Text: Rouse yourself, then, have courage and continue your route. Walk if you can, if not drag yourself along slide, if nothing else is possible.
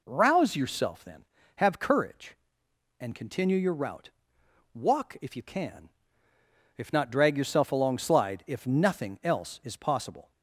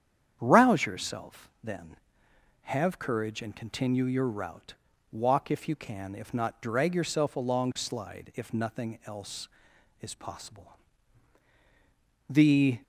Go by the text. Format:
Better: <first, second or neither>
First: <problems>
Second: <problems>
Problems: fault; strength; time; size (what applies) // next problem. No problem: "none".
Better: first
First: none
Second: starts louder than the rest; strong; until 1.4 s; 9 dB // goes on to say "The"; from 12.2 s on; 0.50 s long